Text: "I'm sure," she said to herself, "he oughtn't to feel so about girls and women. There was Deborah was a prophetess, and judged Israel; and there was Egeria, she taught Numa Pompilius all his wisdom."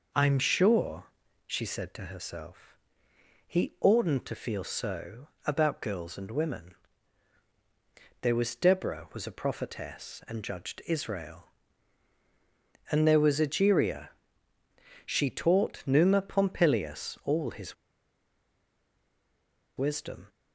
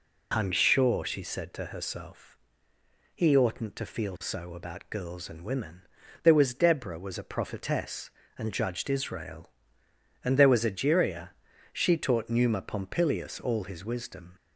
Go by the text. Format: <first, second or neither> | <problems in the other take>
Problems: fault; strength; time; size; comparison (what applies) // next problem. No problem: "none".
second | pauses between "so" and "about"; slight; at 5.2 s; 0.18 s long // pauses between "his" and "wisdom"; strong; at 17.7 s; 2.0 s long